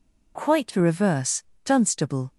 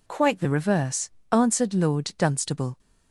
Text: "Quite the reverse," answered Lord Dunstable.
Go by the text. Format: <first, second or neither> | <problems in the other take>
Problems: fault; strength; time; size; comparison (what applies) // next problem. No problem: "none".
second | skips "answered Lord"; at 1.5 s